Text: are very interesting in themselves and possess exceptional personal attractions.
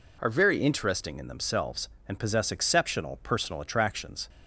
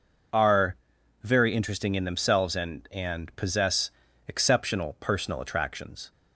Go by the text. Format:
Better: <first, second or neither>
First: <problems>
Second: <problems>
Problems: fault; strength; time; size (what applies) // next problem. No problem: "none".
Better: first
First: none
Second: pauses between "are" and "very"; noticeable; at 0.7 s; 0.48 s long // says "and" twice; at 2.9 s // pauses between "possess" and "exceptional"; slight; at 3.9 s; 0.36 s long